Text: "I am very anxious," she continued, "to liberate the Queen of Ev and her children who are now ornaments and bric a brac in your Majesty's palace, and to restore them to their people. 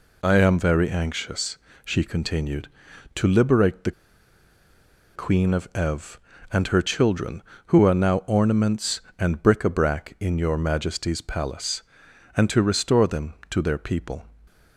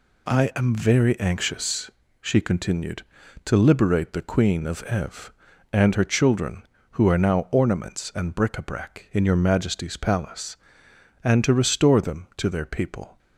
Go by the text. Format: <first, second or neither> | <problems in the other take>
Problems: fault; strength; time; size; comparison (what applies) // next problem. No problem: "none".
second | pauses between "the" and "Queen"; at 3.9 s; 1.2 s long